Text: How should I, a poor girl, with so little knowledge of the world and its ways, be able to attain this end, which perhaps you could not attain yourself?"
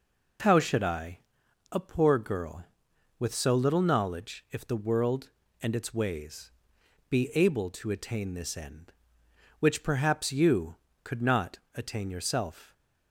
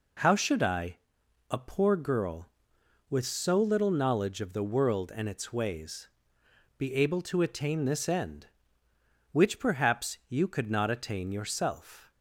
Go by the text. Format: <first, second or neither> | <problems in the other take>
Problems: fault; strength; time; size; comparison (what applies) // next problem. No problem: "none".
second | says "if" for "of"; at 4.5 s // pauses between "not" and "attain"; slight; at 11.5 s; 0.16 s long